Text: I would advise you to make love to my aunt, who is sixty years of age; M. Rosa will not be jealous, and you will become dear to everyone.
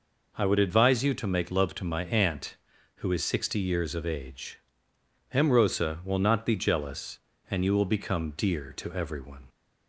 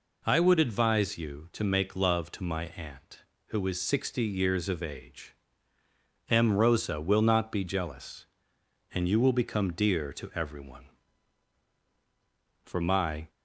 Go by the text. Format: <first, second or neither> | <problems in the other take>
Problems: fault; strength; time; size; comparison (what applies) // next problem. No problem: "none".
first | goes on to say "For my"; noticeable; from 12.6 s on; 0.66 s long